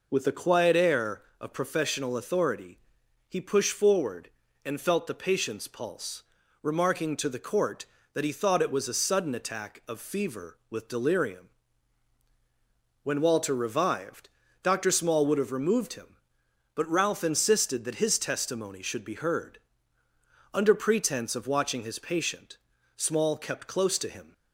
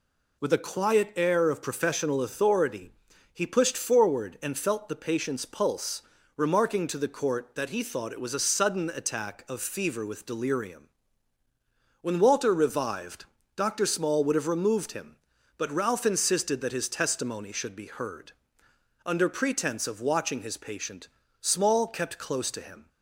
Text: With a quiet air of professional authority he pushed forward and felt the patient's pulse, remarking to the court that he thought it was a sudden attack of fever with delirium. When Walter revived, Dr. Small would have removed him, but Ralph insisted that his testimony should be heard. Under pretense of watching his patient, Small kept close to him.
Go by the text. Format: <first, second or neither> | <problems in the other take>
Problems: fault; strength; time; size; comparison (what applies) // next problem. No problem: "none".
neither | pauses between "authority" and "he"; the same in both